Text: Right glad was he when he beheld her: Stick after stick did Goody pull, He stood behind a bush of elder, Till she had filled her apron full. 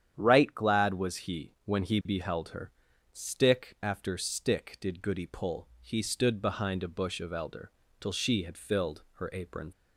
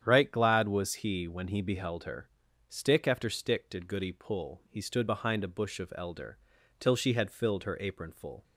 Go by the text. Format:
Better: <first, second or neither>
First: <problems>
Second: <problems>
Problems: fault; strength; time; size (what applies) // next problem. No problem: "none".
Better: second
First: starts louder than the rest; strong; until 1.1 s; 9 dB // stops before "full"; at 9.7 s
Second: starts louder than the rest; strong; until 1.0 s; 9 dB